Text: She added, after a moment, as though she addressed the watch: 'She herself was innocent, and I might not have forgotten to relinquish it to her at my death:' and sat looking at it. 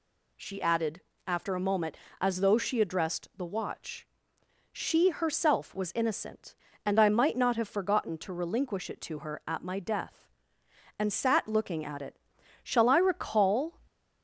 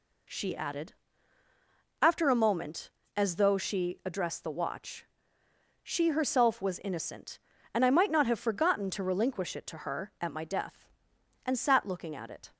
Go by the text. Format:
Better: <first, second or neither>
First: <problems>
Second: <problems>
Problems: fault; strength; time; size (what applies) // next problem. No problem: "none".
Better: second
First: goes on to say "Shall I recall"; noticeable; from 12.6 s on; 1.1 s long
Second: none